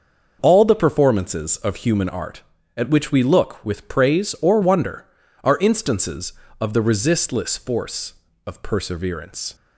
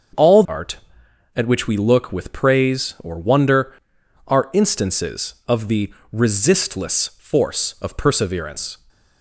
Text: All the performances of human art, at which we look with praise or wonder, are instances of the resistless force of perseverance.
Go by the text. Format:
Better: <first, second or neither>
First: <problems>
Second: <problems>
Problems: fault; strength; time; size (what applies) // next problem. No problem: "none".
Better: first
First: starts louder than the rest; until 1.4 s; 6 dB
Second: starts louder than the rest; until 1.7 s; 6.5 dB // skips "the performances of human"; at 0.4 s // pauses between "the" and "resistless"; slight; at 5.9 s; 0.20 s long